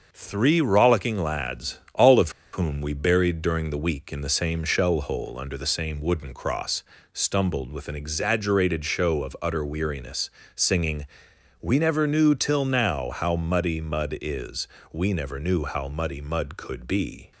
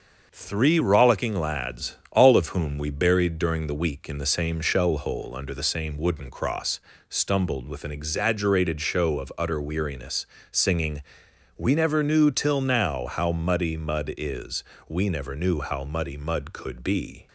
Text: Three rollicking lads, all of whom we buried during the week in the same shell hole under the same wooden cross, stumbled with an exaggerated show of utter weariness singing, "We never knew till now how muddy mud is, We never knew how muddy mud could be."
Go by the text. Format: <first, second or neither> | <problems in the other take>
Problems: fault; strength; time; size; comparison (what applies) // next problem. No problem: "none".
second | starts louder than the rest; until 1.1 s; 6.5 dB; also in the second // pauses between "of" and "whom"; slight; at 2.3 s; 0.22 s long // pauses between "weariness" and "singing"; slight; at 10.2 s; 0.26 s long; slight in the second